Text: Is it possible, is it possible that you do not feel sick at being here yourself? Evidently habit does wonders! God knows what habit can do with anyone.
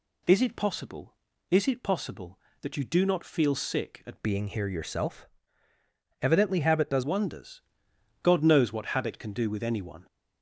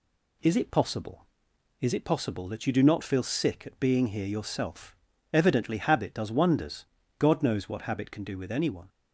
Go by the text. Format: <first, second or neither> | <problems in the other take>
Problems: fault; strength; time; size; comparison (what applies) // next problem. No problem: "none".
second | changes voice from "being" to "does"; from 4.2 to 7.0 s; 2.8 s long